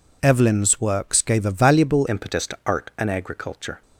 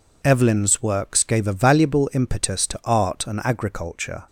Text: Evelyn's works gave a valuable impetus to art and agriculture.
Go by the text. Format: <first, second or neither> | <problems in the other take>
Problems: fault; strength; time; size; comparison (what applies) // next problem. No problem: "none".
second | changes voice at "impetus"; from 2.0 s on; 1.8 s long